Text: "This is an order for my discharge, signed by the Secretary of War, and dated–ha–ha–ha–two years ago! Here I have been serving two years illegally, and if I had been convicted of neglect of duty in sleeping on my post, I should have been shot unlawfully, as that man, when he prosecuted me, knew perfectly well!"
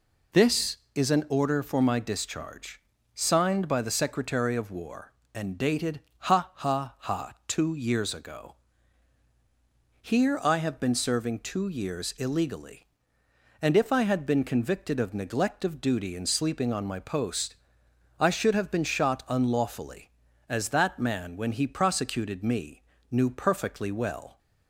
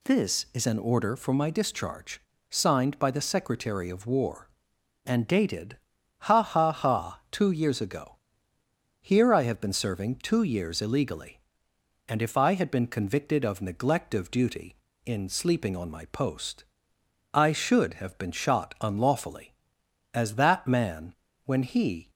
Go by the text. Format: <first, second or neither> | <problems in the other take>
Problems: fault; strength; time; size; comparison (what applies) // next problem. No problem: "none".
first | stops before "prosecuted me knew perfectly well"; at 22.0 s